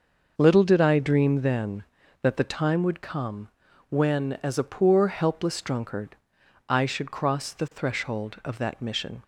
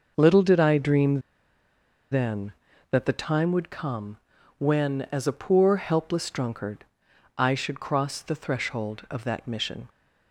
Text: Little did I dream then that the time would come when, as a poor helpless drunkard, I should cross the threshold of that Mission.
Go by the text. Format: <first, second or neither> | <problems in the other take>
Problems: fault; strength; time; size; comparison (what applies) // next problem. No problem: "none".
first | starts louder than the rest; noticeable; until 1.1 s; 6 dB // pauses between "dream" and "then"; noticeable; at 1.1 s; 0.92 s long // pauses between "come" and "when"; at 4.1 s; 0.40 s long; also in the first